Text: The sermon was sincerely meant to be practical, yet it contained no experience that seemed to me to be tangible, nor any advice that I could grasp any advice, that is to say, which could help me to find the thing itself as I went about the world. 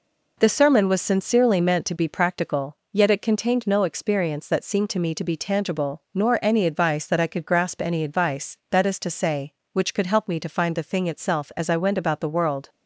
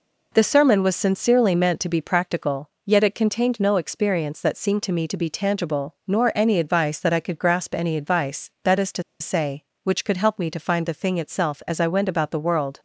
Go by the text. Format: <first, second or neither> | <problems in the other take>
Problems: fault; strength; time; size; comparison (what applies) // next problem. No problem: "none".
first | pauses between "to" and "say"; slight; at 9.0 s; 0.18 s long